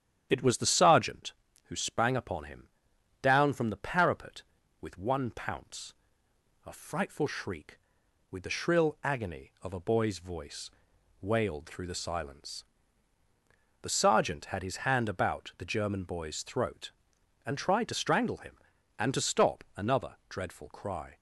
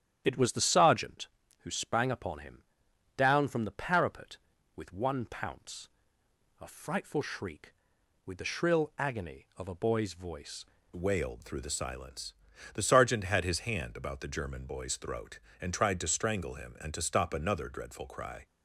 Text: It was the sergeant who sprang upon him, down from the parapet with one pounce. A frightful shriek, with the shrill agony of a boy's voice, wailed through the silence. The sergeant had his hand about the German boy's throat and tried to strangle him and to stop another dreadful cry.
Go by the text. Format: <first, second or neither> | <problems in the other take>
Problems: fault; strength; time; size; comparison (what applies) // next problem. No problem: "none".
first | starts louder than the rest; strong; until 1.2 s; 10 dB; strong in the first // changes voice at "wailed"; from 10.9 s on; 7.5 s long